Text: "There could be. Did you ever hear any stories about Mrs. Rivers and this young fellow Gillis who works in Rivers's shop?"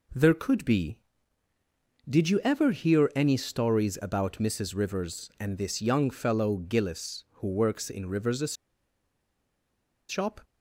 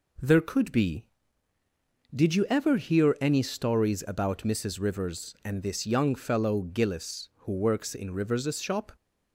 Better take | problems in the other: second | pauses between "Rivers's" and "shop"; strong; at 8.5 s; 1.5 s long

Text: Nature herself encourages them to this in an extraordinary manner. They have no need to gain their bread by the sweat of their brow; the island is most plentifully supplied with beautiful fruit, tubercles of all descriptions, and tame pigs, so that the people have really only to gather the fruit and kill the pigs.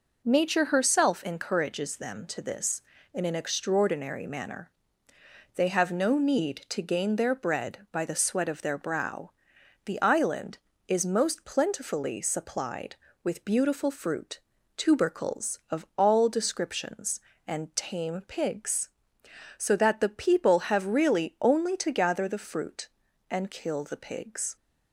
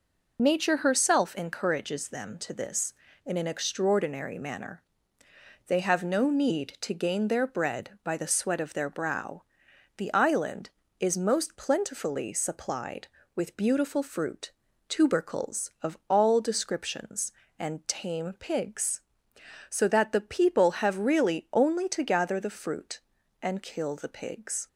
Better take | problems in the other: first | loses the start of "Nature"; at 0.3 s; 45 ms

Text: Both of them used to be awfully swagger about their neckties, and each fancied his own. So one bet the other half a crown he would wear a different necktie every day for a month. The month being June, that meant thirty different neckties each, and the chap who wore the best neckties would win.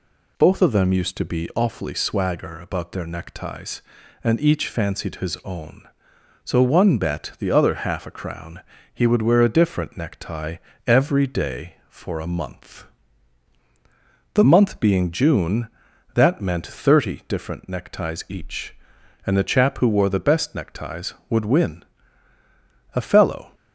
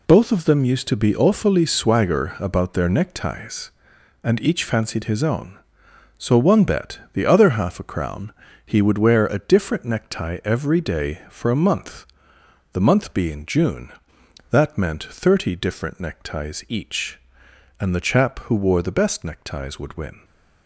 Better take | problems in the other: second | pauses between "crown" and "he"; slight; at 8.5 s; 0.34 s long; slight in the second // pauses between "necktie" and "every"; slight; at 10.5 s; 0.30 s long // goes on to say "A fellow"; from 22.9 s on; 0.58 s long

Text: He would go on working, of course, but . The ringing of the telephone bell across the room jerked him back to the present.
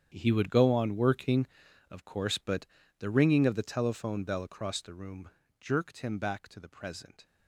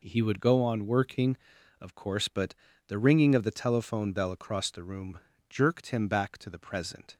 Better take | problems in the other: second | gets quieter; strong; throughout; 15 dB // pauses between "room" and "jerked"; slight; at 5.2 s; 0.30 s long; slight in the second

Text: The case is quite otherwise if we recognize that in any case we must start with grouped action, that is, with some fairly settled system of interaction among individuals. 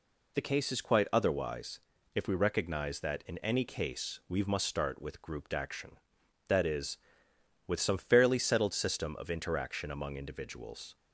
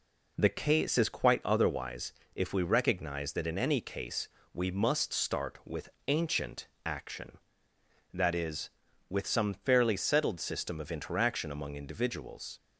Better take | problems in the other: first | pauses between "otherwise" and "if"; slight; at 2.1 s; 0.24 s long; slight in the first // pauses between "case" and "we"; slight; at 4.2 s; 0.26 s long // says "ancient" for "grouped"; at 6.0 s

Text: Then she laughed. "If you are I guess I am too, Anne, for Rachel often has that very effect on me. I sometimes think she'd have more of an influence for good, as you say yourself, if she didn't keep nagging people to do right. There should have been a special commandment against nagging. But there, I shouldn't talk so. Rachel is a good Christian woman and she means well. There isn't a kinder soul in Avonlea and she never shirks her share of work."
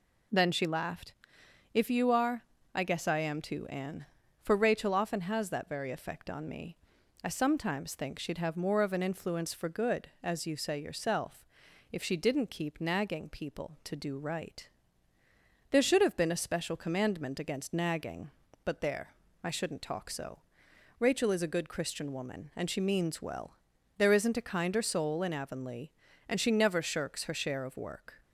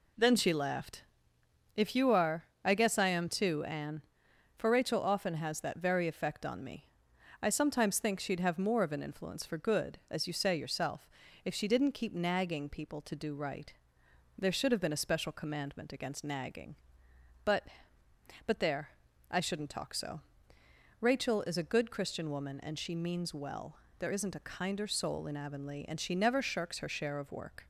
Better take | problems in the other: first | pauses between "are" and "I"; slight; at 2.4 s; 0.20 s long; slight in the first // says "But" twice; at 18.4 s

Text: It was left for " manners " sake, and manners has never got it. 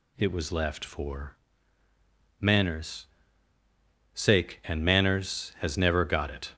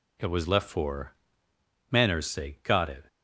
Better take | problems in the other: first | skips "and manners has never"; at 2.6 s

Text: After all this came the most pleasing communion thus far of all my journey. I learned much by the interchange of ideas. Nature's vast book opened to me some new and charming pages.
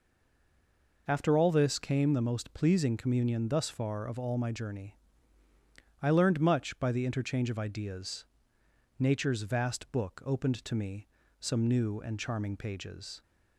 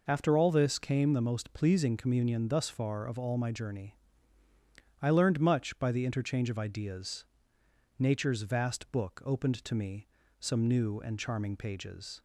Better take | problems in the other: second | stays silent before the first word; until 1.0 s; 1.0 s long // pauses between "me" and "some"; slight; at 11.0 s; 0.32 s long; slight in the second

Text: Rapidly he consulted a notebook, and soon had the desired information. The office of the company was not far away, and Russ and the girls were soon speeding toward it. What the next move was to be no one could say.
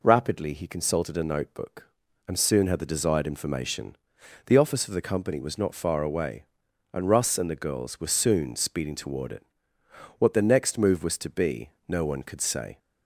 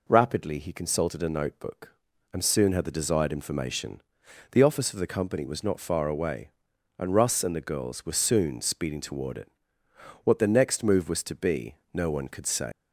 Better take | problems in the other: first | pauses between "be" and "no"; slight; at 11.7 s; 0.18 s long; slight in the first // leaves "say" unfinished; at 12.7 s; 115 ms

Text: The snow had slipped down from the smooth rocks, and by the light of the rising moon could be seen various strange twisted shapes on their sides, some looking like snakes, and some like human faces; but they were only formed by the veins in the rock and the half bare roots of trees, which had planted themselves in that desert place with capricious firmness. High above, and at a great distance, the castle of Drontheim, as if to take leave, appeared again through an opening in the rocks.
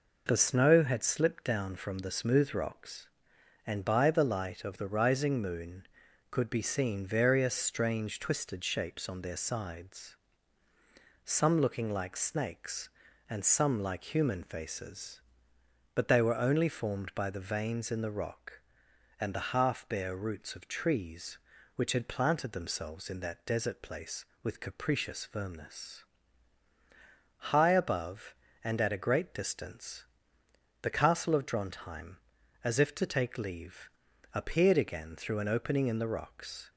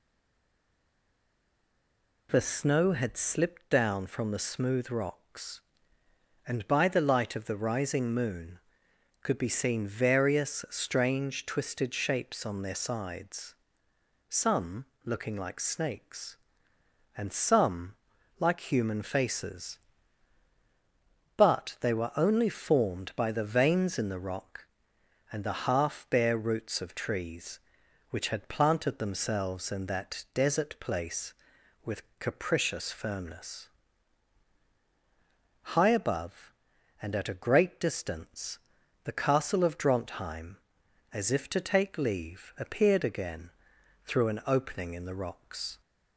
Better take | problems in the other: first | stays silent before the first word; until 2.2 s; 2.2 s long // pauses between "some" and "looking"; slight; at 14.8 s; 0.20 s long // pauses between "some" and "like"; at 17.9 s; 0.44 s long // pauses between "with" and "capricious"; slight; at 32.0 s; 0.16 s long // pauses between "again" and "through"; noticeable; at 43.4 s; 0.56 s long

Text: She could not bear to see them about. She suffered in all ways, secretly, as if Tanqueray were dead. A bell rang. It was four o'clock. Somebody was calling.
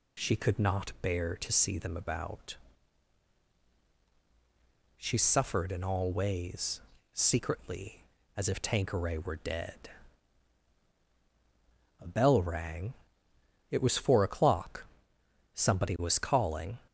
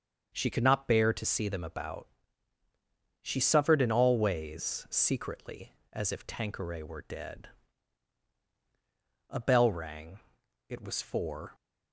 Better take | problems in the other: first | starts louder than the rest; until 1.3 s; 6.5 dB // stops before "o'clock Somebody was calling"; at 11.5 s

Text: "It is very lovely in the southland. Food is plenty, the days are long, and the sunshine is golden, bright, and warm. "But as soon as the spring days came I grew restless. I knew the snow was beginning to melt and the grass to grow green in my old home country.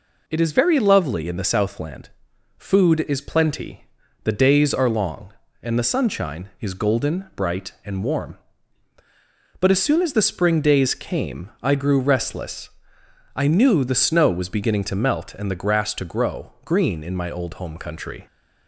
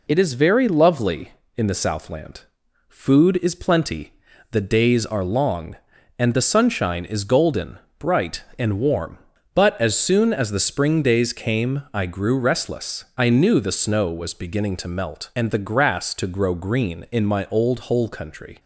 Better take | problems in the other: first | says "hole" for "home"; at 17.7 s

